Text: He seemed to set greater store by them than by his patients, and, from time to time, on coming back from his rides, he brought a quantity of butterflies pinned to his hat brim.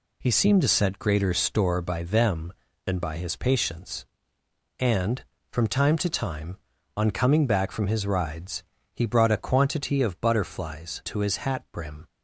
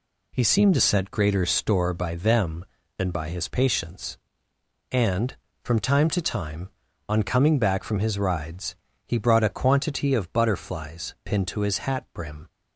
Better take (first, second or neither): second